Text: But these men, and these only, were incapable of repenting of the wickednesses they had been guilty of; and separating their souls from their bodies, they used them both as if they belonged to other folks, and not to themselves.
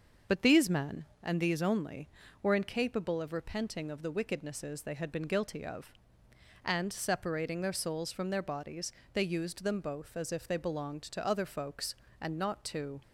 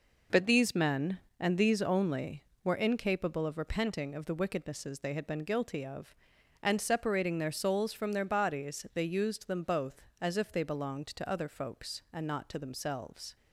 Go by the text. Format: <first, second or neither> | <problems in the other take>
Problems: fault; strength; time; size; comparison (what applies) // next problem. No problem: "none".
second | starts louder than the rest; until 1.4 s; 6.5 dB // stops before "themselves"; at 13.0 s